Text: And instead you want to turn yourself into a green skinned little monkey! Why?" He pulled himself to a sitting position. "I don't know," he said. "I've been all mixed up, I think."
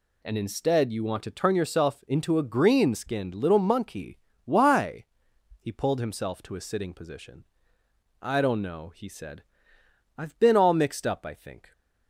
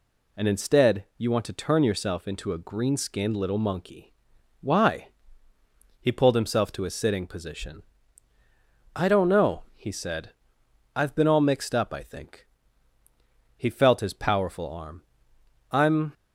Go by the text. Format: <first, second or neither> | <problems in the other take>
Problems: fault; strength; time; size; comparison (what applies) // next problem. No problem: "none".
first | goes on to say "He felt his powerful arm I'm"; strong; from 13.5 s on; 2.5 s long